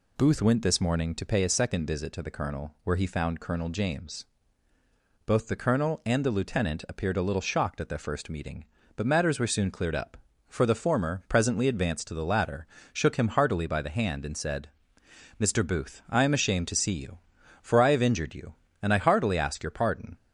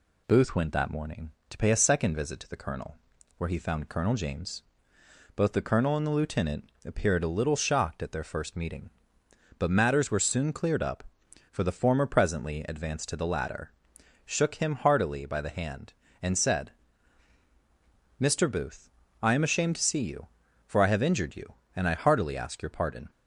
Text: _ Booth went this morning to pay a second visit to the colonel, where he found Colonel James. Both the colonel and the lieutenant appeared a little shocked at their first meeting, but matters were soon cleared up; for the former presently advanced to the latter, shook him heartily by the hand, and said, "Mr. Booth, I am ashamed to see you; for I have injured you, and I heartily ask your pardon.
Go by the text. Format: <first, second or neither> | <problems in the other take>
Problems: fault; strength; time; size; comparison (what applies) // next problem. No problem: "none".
first | says "that" for "this"; at 0.7 s // pauses between "lieutenant" and "appeared"; slight; at 6.6 s; 0.16 s long